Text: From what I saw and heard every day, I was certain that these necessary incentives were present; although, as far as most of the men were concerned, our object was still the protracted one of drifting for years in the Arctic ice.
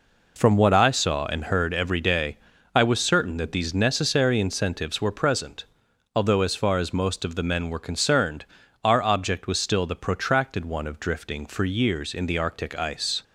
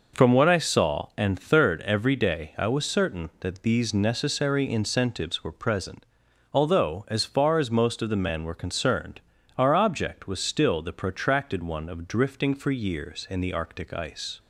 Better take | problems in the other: first | says "third" for "heard"; at 1.3 s

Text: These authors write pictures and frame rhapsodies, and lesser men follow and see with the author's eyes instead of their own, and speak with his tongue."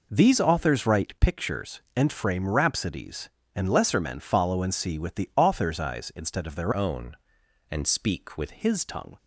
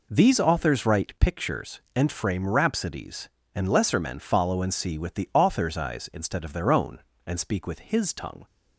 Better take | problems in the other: second | changes voice from "own" to "with"; from 6.7 to 8.4 s; 1.7 s long

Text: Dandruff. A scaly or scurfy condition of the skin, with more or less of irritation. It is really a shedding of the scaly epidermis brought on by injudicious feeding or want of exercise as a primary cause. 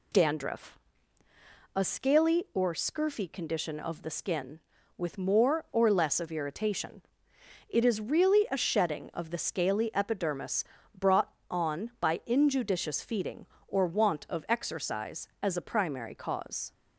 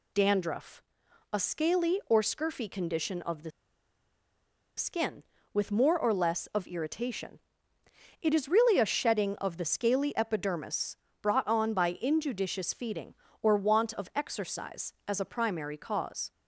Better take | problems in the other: first | pauses between "the" and "skin"; strong; at 3.5 s; 1.2 s long // pauses between "epidermis" and "brought"; slight; at 10.9 s; 0.26 s long; slight in the first

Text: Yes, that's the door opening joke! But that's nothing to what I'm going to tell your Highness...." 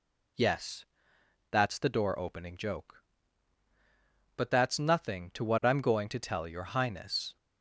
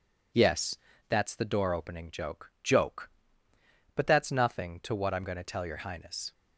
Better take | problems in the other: first | says "joke" twice; at 2.6 s

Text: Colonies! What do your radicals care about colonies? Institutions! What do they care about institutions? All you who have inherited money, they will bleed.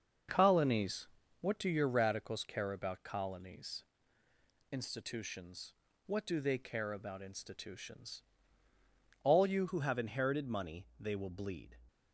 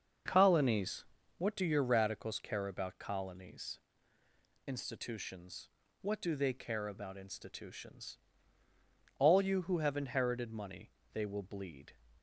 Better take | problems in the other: second | starts louder than the rest; until 1.6 s; 6.5 dB; also in the second // changes voice at "who"; from 9.6 s on; 2.1 s long

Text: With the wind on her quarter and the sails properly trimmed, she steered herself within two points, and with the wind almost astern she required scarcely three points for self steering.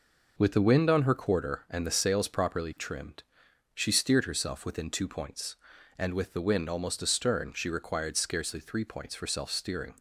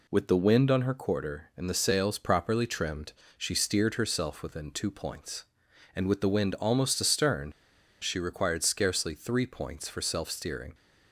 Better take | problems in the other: first | pauses between "astern" and "she"; noticeable; at 7.5 s; 0.50 s long

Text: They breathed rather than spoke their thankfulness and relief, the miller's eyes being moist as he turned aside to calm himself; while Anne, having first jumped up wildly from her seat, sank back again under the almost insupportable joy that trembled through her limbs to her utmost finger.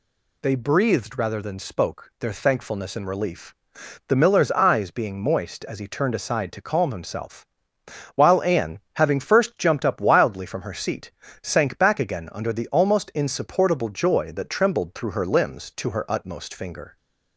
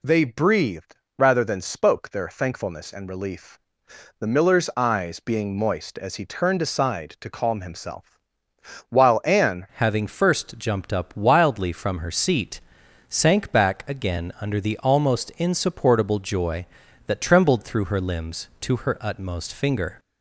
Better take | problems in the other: first | pauses between "breathed" and "rather"; slight; at 0.9 s; 0.20 s long // changes voice at "having"; from 9.7 s on; 10.2 s long

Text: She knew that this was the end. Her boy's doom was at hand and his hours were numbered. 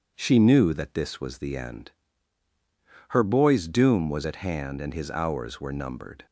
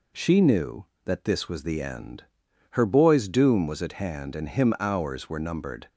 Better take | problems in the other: first | says "him" for "his"; at 4.4 s

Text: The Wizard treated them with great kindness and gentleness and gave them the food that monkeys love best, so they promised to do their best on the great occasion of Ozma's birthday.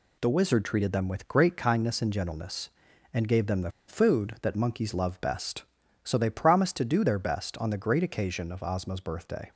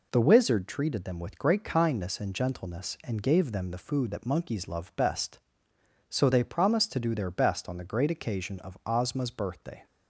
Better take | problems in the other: second | pauses between "the" and "food"; slight; at 3.7 s; 0.17 s long

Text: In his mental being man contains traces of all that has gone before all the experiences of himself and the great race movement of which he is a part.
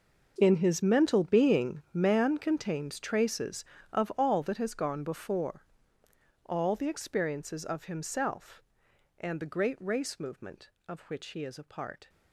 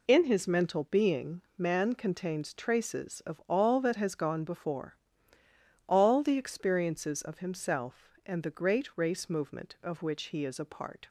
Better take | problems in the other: second | gets quieter; strong; throughout; 16 dB // pauses between "before" and "all"; noticeable; at 5.6 s; 0.82 s long; noticeable in the second

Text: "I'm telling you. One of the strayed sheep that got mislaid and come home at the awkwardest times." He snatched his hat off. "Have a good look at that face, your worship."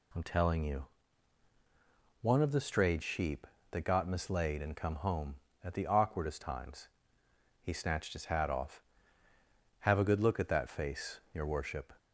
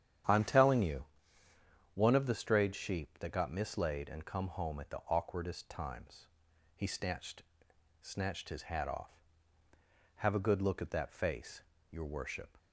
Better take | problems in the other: first | starts louder than the rest; strong; until 2.1 s; 9.5 dB // says "snatched" twice; at 8.0 s

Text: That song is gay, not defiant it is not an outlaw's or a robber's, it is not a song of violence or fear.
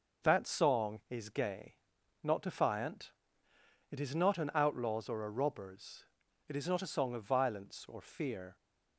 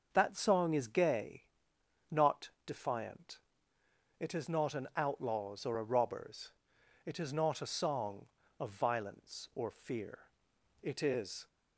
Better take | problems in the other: first | starts louder than the rest; until 1.1 s; 6.5 dB // pauses between "not" and "defiant"; slight; at 2.4 s; 0.18 s long // pauses between "defiant" and "it"; noticeable; at 3.3 s; 0.80 s long; noticeable in the first // goes on to say "It is"; noticeable; from 10.8 s on; 0.64 s long

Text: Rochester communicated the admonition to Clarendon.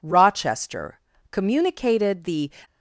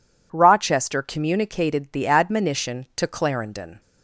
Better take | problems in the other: second | pauses between "Rochester" and "communicated"; slight; at 0.9 s; 0.32 s long // stops before "admonition to Clarendon"; at 2.6 s

